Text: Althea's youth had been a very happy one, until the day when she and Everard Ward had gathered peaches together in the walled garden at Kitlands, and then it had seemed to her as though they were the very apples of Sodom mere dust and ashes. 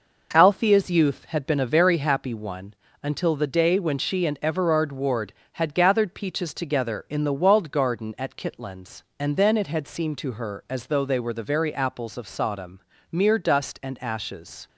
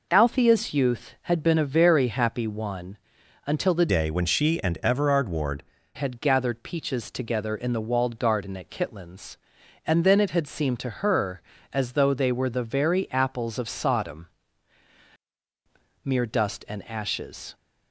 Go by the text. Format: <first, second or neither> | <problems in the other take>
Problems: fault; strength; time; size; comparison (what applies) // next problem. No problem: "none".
first | changes voice from "day" to "Ward"; from 3.8 to 5.6 s; 1.8 s long // pauses between "Sodom" and "mere"; strong; at 14.2 s; 1.8 s long; slight in the first